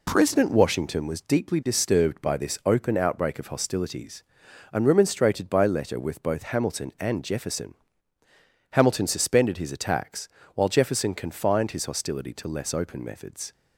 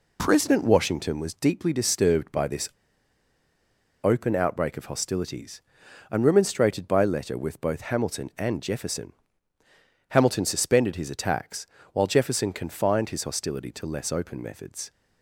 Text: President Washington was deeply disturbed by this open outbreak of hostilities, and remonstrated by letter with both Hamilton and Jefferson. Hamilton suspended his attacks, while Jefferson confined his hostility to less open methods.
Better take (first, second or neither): first